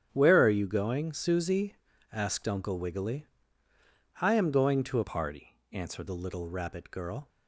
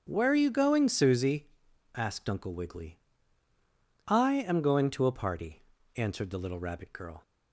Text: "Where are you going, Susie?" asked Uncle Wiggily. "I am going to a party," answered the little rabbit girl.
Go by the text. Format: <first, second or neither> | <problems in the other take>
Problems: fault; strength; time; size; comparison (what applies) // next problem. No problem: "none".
second | starts louder than the rest; strong; until 1.1 s; 9 dB; also in the second // changes voice from "party" to "answered"; from 5.0 to 6.0 s; 1.0 s long